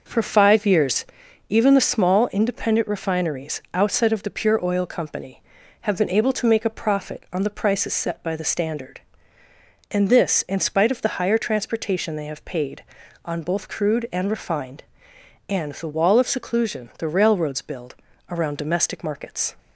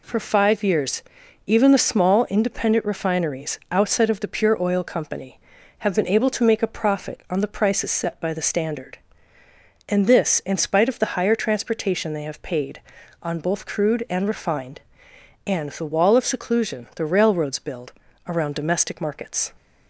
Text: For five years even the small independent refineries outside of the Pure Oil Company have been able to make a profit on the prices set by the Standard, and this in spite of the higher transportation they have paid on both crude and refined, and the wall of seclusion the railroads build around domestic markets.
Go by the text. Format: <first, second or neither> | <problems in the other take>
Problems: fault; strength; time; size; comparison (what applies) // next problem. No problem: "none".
second | starts louder than the rest; noticeable; until 1.2 s; 5.5 dB // pauses between "years" and "even"; at 1.0 s; 0.42 s long; also in the second // pauses between "build" and "around"; slight; at 17.9 s; 0.36 s long; slight in the second